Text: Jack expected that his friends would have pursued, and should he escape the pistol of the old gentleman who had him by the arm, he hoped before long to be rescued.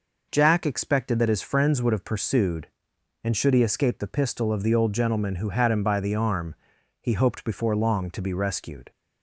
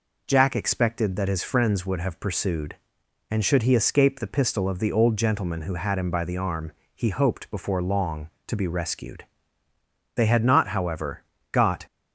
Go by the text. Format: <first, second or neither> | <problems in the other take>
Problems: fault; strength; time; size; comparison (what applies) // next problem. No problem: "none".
first | goes on to say "They had not however got"; strong; from 10.1 s on; 1.7 s long